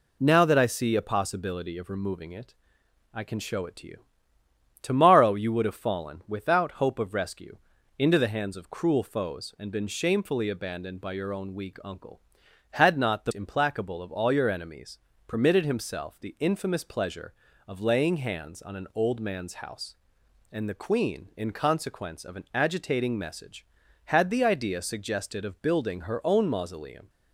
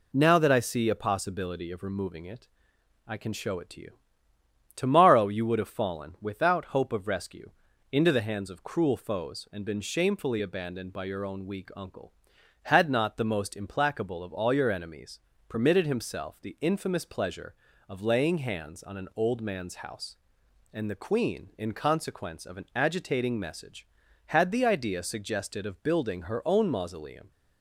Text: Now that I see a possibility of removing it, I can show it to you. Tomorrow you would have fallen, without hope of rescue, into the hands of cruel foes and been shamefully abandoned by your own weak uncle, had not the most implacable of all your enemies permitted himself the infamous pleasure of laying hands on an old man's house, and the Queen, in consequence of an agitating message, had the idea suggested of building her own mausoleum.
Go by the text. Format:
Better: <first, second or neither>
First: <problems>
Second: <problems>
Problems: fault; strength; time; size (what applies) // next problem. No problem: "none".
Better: second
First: skips "most"; at 13.3 s // pauses between "enemies" and "permitted"; slight; at 14.9 s; 0.26 s long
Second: pauses between "enemies" and "permitted"; slight; at 15.2 s; 0.26 s long